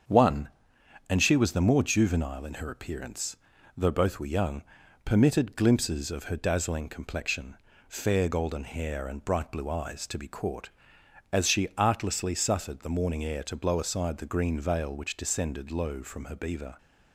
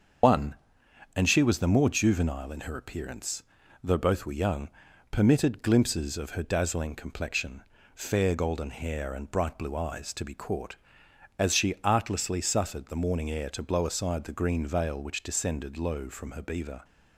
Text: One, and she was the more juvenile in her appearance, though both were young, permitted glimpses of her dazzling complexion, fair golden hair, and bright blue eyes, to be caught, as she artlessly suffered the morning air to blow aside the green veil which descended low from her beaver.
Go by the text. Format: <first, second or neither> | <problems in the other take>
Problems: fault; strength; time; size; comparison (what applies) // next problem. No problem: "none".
first | loses the start of "One"; at 0.2 s; 105 ms // starts louder than the rest; until 1.8 s; 6.5 dB; strong in the first